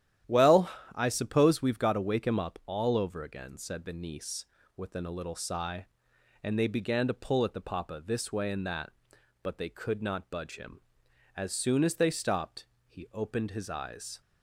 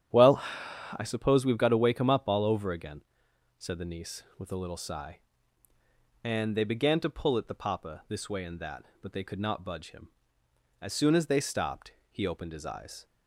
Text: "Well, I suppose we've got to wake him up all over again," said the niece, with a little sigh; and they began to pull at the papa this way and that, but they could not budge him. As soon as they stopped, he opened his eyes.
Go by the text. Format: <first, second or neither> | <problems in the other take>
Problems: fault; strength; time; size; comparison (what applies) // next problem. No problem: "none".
second | starts louder than the rest; strong; until 1.5 s; 11.5 dB; strong in the second // says "within" for "with"; at 4.7 s